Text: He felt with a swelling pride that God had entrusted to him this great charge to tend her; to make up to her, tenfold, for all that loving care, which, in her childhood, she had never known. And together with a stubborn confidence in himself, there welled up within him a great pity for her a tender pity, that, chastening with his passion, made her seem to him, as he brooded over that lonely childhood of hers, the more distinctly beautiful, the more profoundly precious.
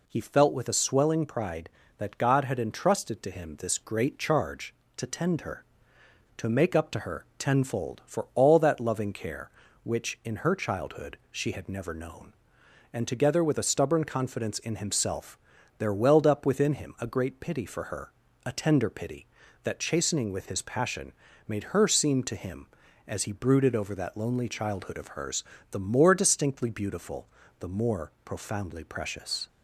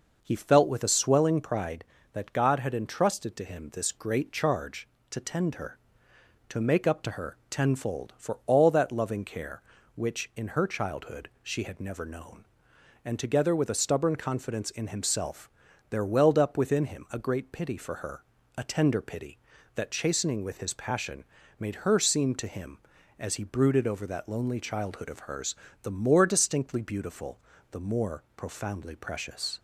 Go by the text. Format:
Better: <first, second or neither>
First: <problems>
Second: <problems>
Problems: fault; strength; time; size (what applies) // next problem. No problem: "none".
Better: first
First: pauses between "her" and "a"; slight; at 18.1 s; 0.36 s long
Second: starts louder than the rest; noticeable; until 1.8 s; 5.5 dB // pauses between "her" and "a"; slight; at 18.2 s; 0.36 s long